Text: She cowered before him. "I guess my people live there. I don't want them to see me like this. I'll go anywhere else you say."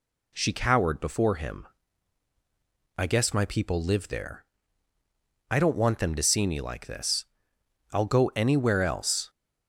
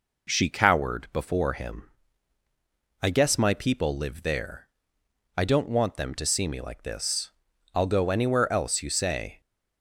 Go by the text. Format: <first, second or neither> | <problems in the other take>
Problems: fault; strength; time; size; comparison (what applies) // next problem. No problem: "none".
second | stops before "you say"; at 9.2 s